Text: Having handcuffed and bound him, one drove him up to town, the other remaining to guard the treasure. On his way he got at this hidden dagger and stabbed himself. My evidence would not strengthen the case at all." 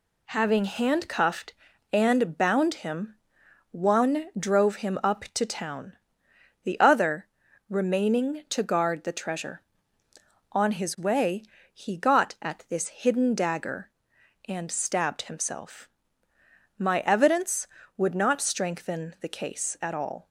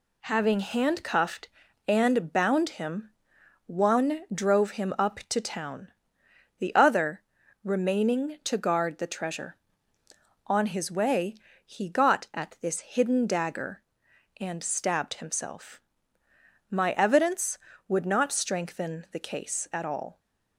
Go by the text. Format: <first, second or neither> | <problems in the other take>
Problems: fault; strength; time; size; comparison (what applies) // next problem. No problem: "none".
neither | pauses between "other" and "remaining"; the same in both // pauses between "way" and "he"; slight; the same in both